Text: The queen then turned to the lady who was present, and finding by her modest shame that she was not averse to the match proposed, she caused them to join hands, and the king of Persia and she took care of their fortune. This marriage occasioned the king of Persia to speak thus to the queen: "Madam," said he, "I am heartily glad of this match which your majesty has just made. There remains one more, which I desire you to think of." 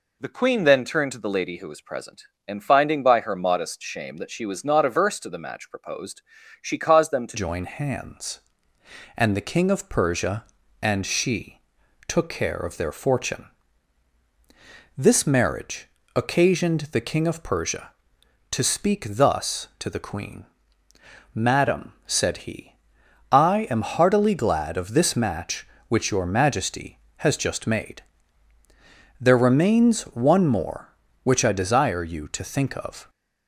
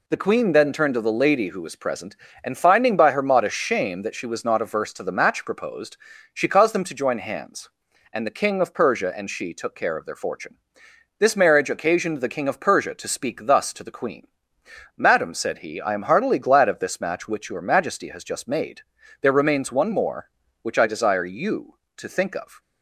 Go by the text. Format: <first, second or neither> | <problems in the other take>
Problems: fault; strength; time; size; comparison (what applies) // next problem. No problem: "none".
second | changes voice at "join"; from 7.3 s on; 25.7 s long // pauses between "she" and "took"; noticeable; at 11.5 s; 0.48 s long // pauses between "marriage" and "occasioned"; slight; at 15.8 s; 0.26 s long